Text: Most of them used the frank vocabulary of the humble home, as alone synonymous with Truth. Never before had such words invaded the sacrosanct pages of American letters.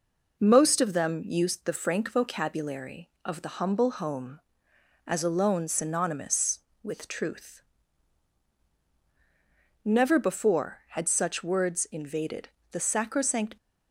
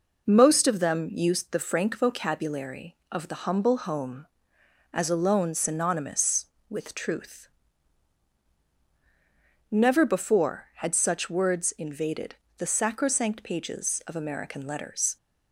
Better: second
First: pauses between "invaded" and "the"; slight; at 12.5 s; 0.20 s long // stops before "pages of American letters"; at 13.5 s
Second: pauses between "invaded" and "the"; slight; at 12.3 s; 0.20 s long

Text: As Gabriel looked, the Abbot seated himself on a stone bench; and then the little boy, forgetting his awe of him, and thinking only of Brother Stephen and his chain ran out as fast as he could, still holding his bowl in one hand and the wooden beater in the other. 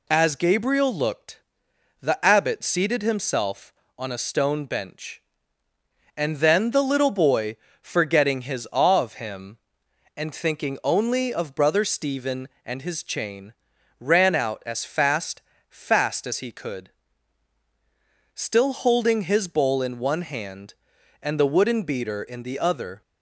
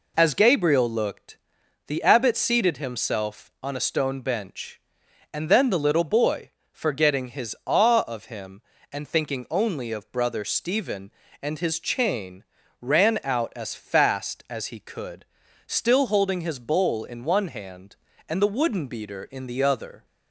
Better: second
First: pauses between "chain" and "ran"; noticeable; at 13.5 s; 0.46 s long // says "fast" twice; at 15.6 s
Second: pauses between "chain" and "ran"; slight; at 12.4 s; 0.34 s long

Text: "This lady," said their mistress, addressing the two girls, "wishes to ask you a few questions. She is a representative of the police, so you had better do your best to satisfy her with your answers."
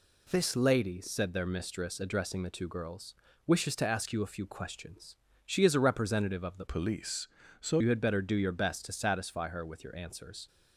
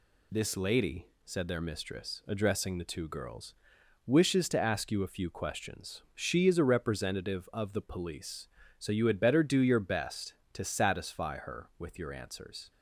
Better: second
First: changes voice from "police" to "so"; from 6.6 to 7.7 s; 1.1 s long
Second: none

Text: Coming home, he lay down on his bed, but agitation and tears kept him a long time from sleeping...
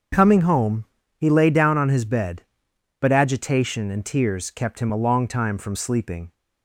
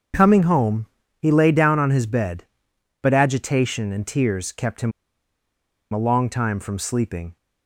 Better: first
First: starts louder than the rest; until 1.4 s; 7 dB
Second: starts louder than the rest; until 1.4 s; 7 dB // pauses between "him" and "a"; at 4.9 s; 1.0 s long

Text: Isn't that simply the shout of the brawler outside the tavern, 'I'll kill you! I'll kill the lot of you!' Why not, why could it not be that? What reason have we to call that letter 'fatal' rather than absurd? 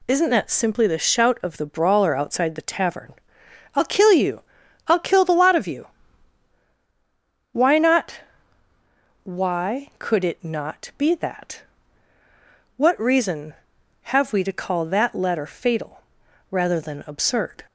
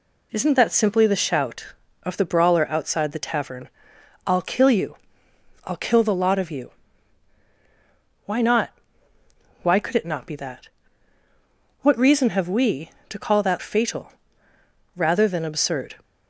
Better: first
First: pauses between "fatal" and "rather"; noticeable; at 16.0 s; 0.48 s long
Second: skips "letter"; at 13.5 s // pauses between "fatal" and "rather"; noticeable; at 14.1 s; 0.82 s long

